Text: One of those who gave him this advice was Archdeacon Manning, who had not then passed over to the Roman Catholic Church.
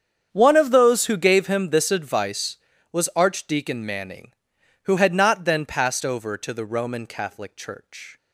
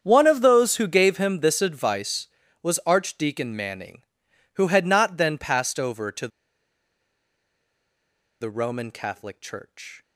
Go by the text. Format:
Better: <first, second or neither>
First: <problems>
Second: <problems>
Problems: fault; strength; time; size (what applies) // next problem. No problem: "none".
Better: first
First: starts louder than the rest; strong; until 1.3 s; 8 dB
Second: starts louder than the rest; strong; until 1.0 s; 8 dB // pauses between "to" and "the"; strong; at 6.2 s; 2.1 s long